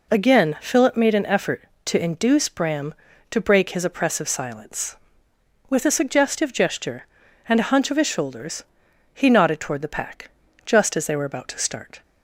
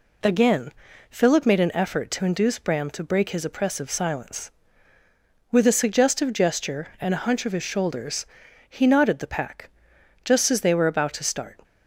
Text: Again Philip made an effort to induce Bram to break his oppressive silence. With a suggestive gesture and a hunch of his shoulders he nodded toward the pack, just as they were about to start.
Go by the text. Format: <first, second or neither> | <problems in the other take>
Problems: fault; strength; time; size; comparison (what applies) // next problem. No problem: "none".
first | pauses between "Again" and "Philip"; slight; at 0.7 s; 0.36 s long // pauses between "shoulders" and "he"; at 8.2 s; 0.44 s long; noticeable in the first // skips "toward"; at 9.1 s